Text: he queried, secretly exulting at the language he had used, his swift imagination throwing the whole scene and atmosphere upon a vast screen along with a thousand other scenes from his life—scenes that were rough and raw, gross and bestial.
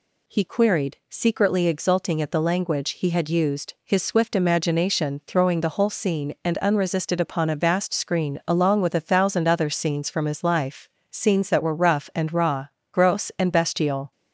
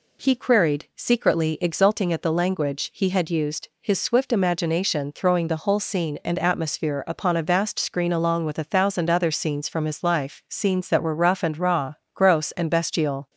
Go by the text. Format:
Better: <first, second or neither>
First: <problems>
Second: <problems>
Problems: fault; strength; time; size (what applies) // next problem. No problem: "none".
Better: second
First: says "unresisted" for "atmosphere"; at 6.5 s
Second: none